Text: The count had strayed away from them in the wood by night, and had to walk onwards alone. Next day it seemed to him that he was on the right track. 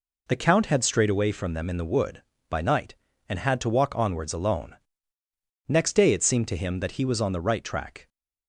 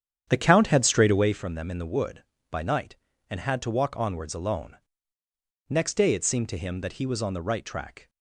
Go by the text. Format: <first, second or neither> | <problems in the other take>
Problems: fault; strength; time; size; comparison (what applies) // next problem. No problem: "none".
first | starts louder than the rest; strong; until 1.4 s; 9 dB